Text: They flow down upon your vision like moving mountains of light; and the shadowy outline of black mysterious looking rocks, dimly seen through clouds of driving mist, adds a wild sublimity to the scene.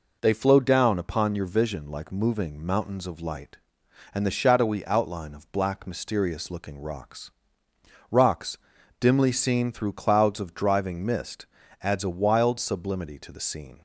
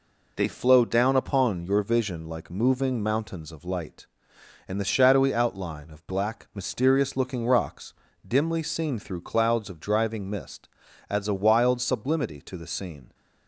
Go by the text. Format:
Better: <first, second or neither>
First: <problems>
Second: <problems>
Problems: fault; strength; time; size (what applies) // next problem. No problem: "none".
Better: second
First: says "rocks" twice; at 8.0 s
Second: none